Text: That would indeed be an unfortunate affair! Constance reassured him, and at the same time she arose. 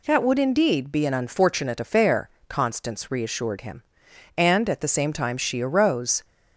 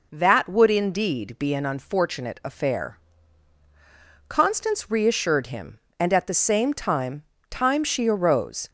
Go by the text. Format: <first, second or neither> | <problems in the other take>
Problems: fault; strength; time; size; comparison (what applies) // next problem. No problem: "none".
first | says "time" twice; at 7.4 s